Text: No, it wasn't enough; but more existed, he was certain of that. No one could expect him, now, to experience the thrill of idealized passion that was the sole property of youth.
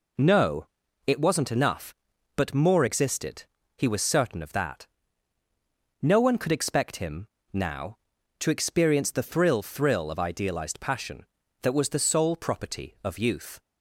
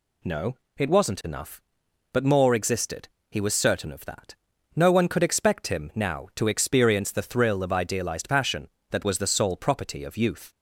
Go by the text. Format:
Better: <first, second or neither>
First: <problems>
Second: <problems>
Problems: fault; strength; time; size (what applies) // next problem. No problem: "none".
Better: second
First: says "thrill" twice; at 9.6 s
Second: none